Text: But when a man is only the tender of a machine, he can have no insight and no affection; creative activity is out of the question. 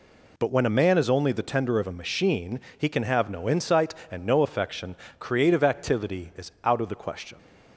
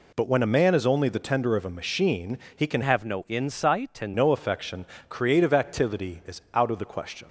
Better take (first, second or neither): first